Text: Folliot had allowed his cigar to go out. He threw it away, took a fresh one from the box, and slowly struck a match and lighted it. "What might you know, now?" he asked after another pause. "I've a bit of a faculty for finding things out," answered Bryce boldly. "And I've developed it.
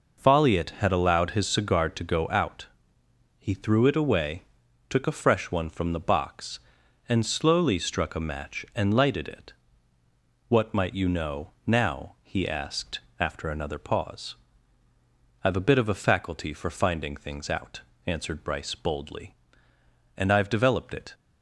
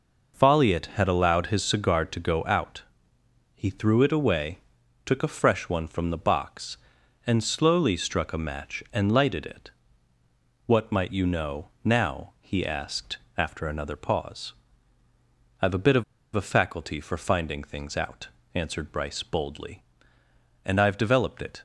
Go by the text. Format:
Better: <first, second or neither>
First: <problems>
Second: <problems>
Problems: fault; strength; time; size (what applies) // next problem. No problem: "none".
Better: first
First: pauses between "asked" and "after"; slight; at 12.9 s; 0.20 s long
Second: pauses between "asked" and "after"; slight; at 13.1 s; 0.20 s long // pauses between "of" and "a"; slight; at 16.0 s; 0.30 s long